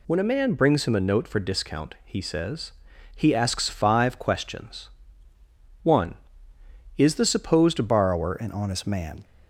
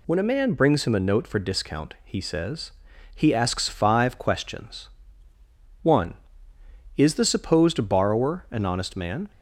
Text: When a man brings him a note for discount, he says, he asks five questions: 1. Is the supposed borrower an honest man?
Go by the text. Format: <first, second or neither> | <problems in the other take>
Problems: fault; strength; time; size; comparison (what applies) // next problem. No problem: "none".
second | changes voice at "borrower"; from 7.8 s on; 1.4 s long